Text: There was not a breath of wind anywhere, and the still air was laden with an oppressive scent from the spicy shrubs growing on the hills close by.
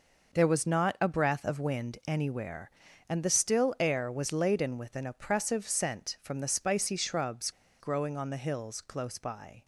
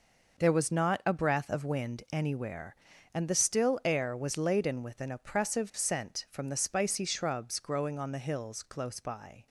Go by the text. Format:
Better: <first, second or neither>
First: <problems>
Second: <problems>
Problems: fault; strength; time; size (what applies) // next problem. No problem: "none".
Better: second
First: pauses between "shrubs" and "growing"; slight; at 7.4 s; 0.30 s long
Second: none